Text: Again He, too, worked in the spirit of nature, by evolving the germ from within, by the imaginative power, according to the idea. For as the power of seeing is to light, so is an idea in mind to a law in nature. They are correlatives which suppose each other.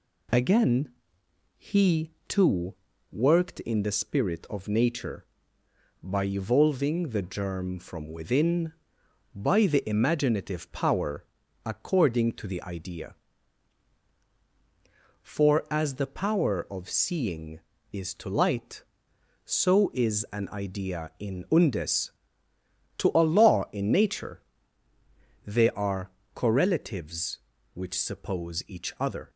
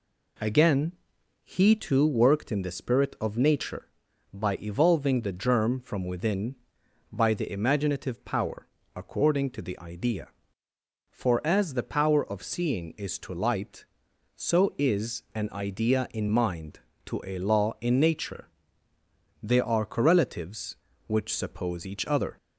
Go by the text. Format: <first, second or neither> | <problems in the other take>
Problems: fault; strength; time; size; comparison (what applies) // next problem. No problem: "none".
second | pauses between "Again" and "He"; noticeable; at 0.8 s; 0.68 s long; noticeable in the second // says "undes" for "mind"; at 21.4 s // pauses between "are" and "correlatives"; slight; at 26.0 s; 0.24 s long